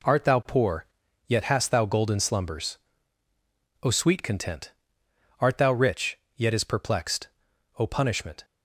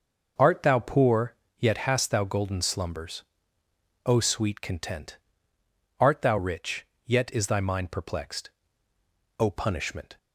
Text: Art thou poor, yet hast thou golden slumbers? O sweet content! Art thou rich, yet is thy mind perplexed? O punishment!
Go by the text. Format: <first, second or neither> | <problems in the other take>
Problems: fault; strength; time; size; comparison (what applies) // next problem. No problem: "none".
second | skips "thy mind"; at 6.6 s